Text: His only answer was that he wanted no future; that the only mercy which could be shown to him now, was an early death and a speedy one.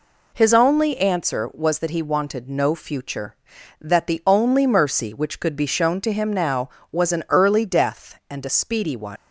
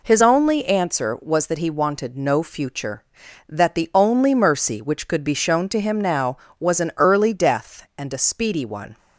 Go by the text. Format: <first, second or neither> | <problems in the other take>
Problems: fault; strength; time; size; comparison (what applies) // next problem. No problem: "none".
second | leaves "one" unfinished; at 9.1 s; 115 ms